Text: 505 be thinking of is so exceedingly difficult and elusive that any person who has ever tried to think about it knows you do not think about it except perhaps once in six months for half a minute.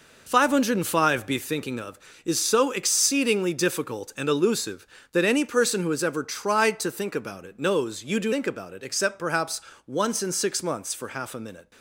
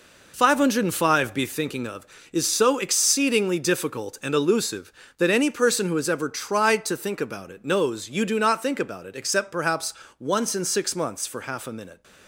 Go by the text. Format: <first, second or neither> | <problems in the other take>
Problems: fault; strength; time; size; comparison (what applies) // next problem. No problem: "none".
second | skips "not"; at 8.3 s // pauses between "perhaps" and "once"; slight; at 9.6 s; 0.26 s long; slight in the second